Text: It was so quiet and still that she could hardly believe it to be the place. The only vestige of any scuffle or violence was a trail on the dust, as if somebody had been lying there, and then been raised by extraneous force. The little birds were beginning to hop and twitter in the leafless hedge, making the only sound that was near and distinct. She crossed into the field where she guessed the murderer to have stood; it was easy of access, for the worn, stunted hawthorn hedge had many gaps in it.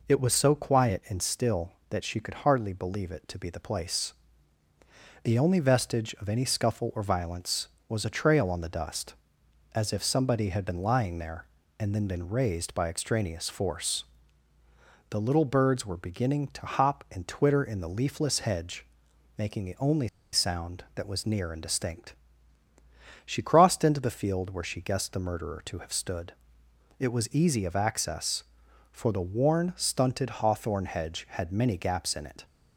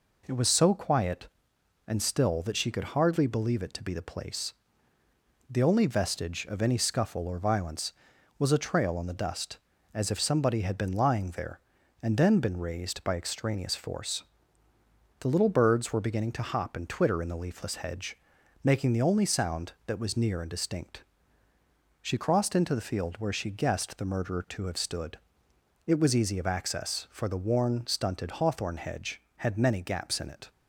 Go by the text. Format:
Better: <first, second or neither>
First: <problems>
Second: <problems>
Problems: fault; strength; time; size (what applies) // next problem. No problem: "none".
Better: second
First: pauses between "only" and "sound"; slight; at 20.0 s; 0.25 s long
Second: none